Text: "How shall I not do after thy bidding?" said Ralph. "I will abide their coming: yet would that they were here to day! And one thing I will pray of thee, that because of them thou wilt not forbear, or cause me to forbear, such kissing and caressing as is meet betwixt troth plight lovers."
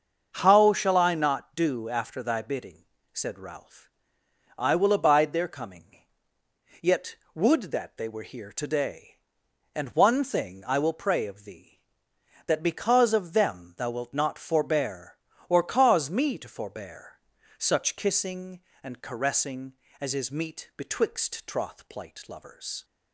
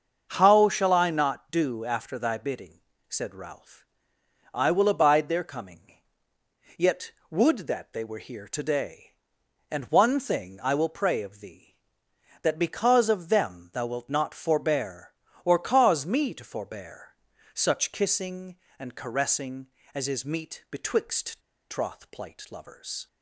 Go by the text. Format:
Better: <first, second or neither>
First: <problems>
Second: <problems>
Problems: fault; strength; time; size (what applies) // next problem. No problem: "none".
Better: first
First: starts louder than the rest; until 1.3 s; 6.5 dB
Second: starts louder than the rest; until 1.3 s; 6.5 dB // pauses between "betwixt" and "troth"; slight; at 21.4 s; 0.29 s long